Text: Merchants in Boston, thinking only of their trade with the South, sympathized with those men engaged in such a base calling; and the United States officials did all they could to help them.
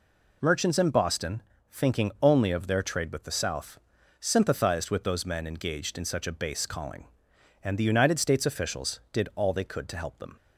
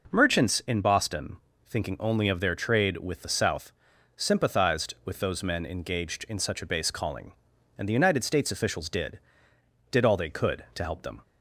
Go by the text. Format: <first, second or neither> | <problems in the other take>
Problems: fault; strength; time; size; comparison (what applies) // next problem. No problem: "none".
first | says "did" twice; at 9.8 s